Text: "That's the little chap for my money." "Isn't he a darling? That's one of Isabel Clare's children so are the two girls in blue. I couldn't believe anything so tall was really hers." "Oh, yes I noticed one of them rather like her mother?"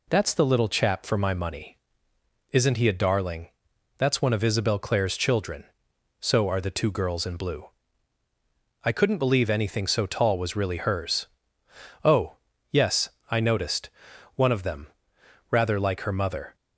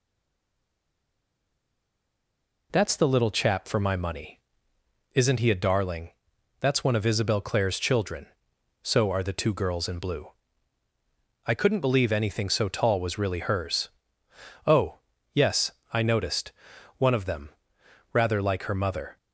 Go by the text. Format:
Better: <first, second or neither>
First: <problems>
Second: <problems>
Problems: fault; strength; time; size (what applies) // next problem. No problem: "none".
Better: first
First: pauses between "yes" and "I"; slight; at 13.1 s; 0.20 s long // pauses between "noticed" and "one"; at 13.9 s; 0.44 s long // pauses between "them" and "rather"; noticeable; at 14.8 s; 0.64 s long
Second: stays silent before the first word; strong; until 2.7 s; 2.7 s long // pauses between "yes" and "I"; slight; at 15.7 s; 0.20 s long // pauses between "noticed" and "one"; at 16.5 s; 0.44 s long // pauses between "them" and "rather"; noticeable; at 17.4 s; 0.64 s long